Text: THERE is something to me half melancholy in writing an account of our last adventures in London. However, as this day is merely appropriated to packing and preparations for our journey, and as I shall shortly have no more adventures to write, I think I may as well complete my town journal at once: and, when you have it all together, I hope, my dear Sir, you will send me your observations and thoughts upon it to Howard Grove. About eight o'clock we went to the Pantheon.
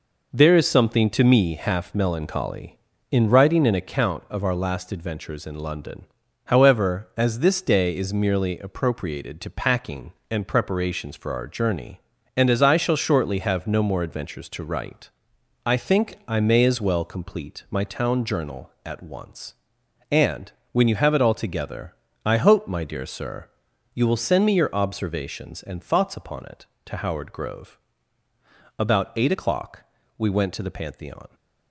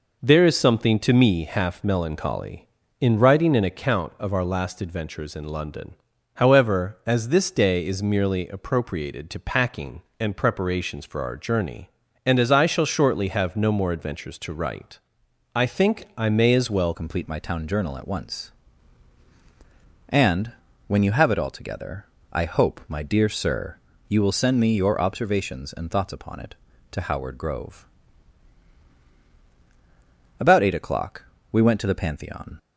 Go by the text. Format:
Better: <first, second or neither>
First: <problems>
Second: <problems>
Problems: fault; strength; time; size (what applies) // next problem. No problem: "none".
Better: first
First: pauses between "o'clock" and "we"; slight; at 29.8 s; 0.34 s long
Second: changes voice at "complete"; from 16.9 s on; 15.6 s long // pauses between "o'clock" and "we"; slight; at 31.2 s; 0.30 s long